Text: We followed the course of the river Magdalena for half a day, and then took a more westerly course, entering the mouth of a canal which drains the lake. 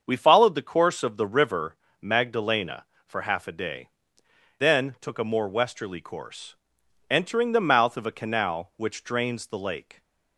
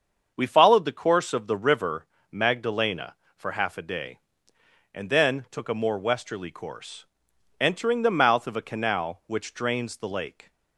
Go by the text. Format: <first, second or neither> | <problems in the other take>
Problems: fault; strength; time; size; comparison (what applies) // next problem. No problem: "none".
second | starts louder than the rest; until 1.0 s; 7 dB; also in the second // pauses between "river" and "Magdalena"; slight; at 1.7 s; 0.26 s long; slight in the second // skips "and"; at 4.2 s